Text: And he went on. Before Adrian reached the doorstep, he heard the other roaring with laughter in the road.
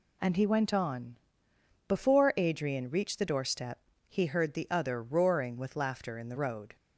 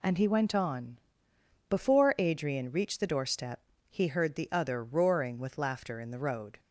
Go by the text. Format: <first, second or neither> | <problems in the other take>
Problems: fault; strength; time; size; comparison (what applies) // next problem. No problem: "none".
neither | none